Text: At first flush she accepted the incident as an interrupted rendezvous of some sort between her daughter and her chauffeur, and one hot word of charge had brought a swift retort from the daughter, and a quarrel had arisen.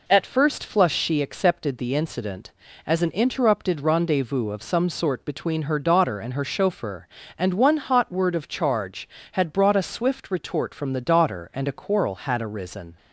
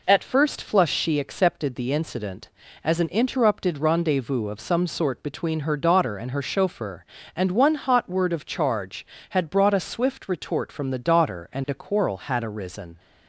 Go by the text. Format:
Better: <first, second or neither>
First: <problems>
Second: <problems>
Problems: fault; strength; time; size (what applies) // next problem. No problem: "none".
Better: neither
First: none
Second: none